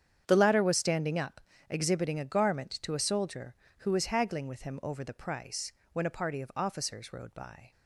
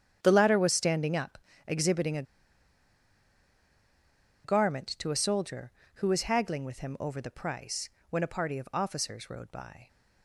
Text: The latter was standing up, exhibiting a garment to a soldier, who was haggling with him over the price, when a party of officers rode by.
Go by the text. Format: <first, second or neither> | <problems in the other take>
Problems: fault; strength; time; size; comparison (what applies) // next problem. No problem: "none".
first | starts louder than the rest; strong; until 1.2 s; 8.5 dB; strong in the first // pauses between "a" and "garment"; strong; at 2.2 s; 2.2 s long